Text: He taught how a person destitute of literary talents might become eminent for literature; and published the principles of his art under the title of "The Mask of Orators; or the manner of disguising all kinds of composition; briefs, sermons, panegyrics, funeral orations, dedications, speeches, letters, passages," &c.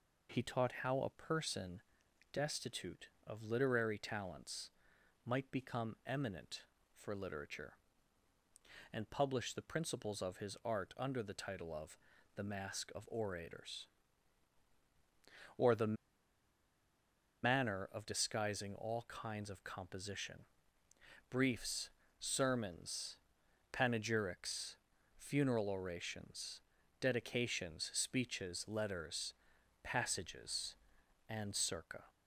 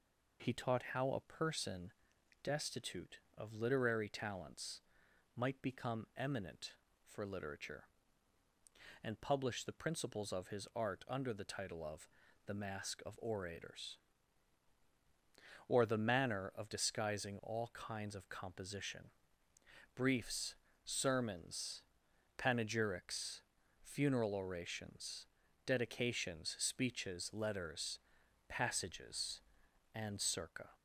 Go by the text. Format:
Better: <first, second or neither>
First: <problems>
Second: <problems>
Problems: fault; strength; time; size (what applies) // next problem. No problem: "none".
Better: second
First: pauses between "person" and "destitute"; noticeable; at 1.8 s; 0.52 s long // pauses between "talents" and "might"; noticeable; at 4.7 s; 0.56 s long // pauses between "of" and "The"; at 11.9 s; 0.40 s long // pauses between "the" and "manner"; strong; at 15.9 s; 1.4 s long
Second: pauses between "person" and "destitute"; noticeable; at 1.9 s; 0.52 s long // pauses between "talents" and "might"; noticeable; at 4.8 s; 0.56 s long // pauses between "of" and "The"; at 12.0 s; 0.40 s long